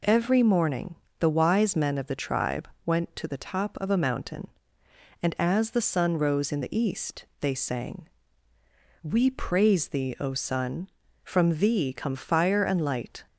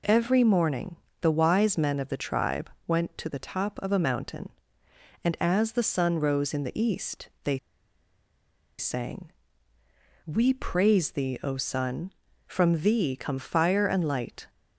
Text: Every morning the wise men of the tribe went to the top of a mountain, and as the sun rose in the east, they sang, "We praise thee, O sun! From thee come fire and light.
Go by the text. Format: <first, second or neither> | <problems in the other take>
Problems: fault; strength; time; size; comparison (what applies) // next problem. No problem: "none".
first | pauses between "morning" and "the"; slight; at 0.9 s; 0.26 s long; slight in the first // pauses between "tribe" and "went"; slight; at 2.6 s; 0.18 s long; slight in the first // pauses between "they" and "sang"; at 7.5 s; 1.2 s long